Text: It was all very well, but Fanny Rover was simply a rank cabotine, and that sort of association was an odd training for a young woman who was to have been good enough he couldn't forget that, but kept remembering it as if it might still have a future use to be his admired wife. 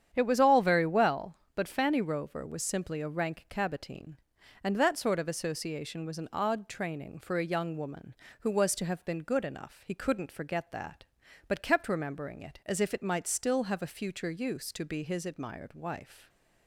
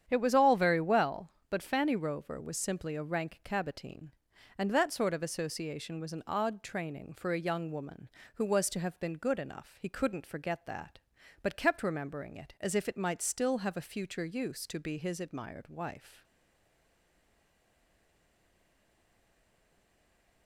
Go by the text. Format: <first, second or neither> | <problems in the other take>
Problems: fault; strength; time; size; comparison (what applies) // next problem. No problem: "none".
first | starts louder than the rest; strong; until 1.1 s; 9 dB; strong in the first // stays silent after the last word; strong; from 16.2 s on; 4.2 s long